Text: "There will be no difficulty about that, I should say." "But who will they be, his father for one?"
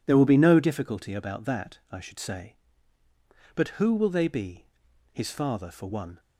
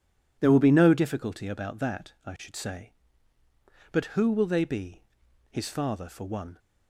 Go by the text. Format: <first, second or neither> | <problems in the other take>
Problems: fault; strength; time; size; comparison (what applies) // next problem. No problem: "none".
neither | none